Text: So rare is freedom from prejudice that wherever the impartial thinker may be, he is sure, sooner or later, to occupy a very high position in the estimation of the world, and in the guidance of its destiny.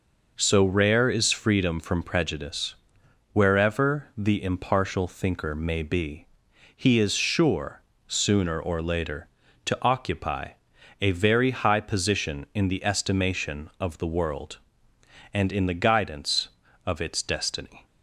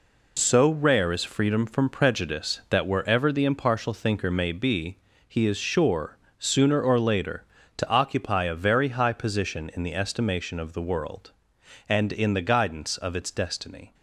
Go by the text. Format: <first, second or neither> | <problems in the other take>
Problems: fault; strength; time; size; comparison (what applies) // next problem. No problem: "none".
second | skips "that"; at 3.0 s // pauses between "occupy" and "a"; noticeable; at 10.5 s; 0.50 s long